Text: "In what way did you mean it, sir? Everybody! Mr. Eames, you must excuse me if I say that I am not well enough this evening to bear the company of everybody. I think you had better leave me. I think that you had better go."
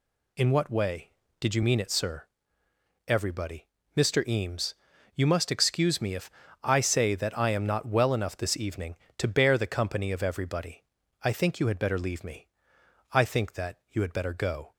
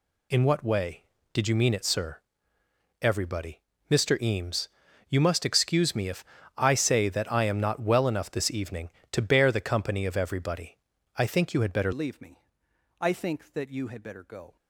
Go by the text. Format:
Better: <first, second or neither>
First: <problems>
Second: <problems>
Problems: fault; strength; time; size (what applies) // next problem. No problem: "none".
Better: first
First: pauses between "if" and "I"; slight; at 6.3 s; 0.32 s long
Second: pauses between "if" and "I"; slight; at 6.2 s; 0.32 s long // changes voice at "leave"; from 11.9 s on; 2.6 s long